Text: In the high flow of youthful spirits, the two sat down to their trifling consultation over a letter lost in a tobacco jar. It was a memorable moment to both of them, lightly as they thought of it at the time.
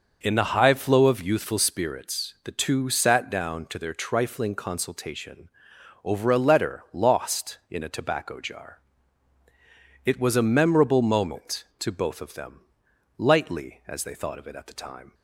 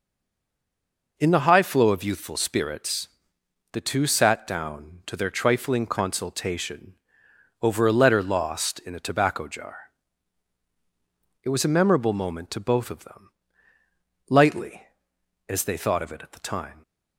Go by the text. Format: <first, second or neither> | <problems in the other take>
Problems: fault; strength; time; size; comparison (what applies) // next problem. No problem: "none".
first | stays silent before the first word; noticeable; until 1.1 s; 1.1 s long // pauses between "consultation" and "over"; noticeable; at 6.9 s; 0.66 s long; noticeable in the first